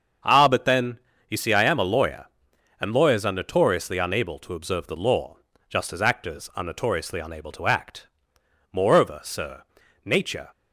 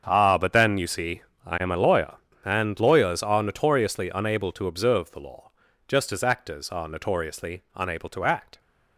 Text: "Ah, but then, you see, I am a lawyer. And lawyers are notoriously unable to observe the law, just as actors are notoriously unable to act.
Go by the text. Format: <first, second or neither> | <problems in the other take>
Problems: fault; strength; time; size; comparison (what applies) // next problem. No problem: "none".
second | starts louder than the rest; until 1.5 s; 7 dB; strong in the second // goes on to say "Moreover sir Nature"; strong; from 8.7 s on; 1.7 s long